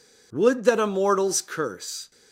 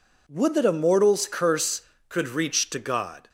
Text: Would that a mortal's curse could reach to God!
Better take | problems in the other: second | stops before "could reach to God"; at 2.1 s

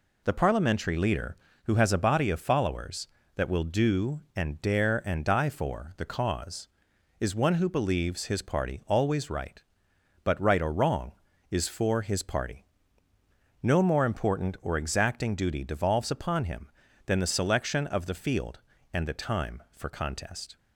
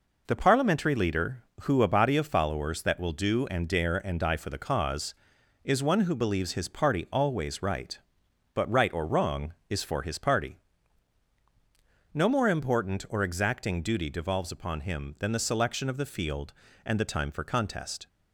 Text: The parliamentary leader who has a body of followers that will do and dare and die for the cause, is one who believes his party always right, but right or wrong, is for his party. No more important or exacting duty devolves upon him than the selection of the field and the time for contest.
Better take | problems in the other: first | skips "has"; at 1.8 s

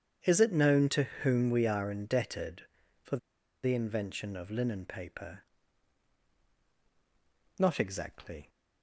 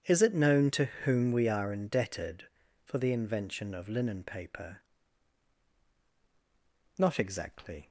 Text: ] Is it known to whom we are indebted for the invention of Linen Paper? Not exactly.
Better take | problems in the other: second | starts louder than the rest; strong; until 1.2 s; 8 dB; strong in the second // pauses between "for" and "the"; noticeable; at 3.1 s; 0.46 s long

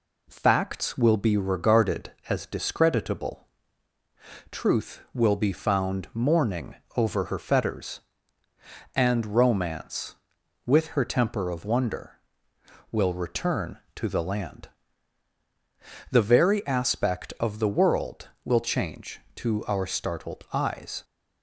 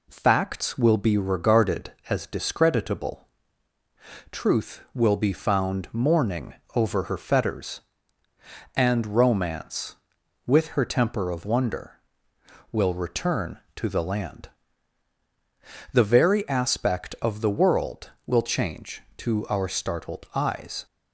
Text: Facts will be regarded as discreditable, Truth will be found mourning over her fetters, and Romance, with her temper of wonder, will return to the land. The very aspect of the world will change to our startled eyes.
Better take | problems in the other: neither | pauses between "mourning" and "over"; slight; the same in both

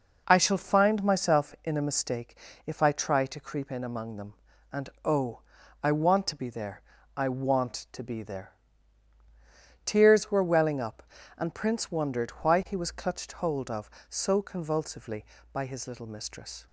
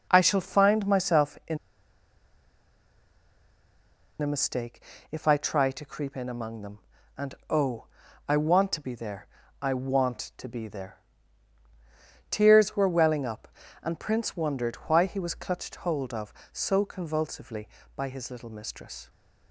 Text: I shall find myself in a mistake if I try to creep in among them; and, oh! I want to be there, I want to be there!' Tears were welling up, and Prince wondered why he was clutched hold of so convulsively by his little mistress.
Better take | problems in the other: first | pauses between "in" and "a"; strong; at 1.5 s; 2.6 s long // pauses between "mistake" and "if"; slight; at 4.8 s; 0.28 s long; slight in the first

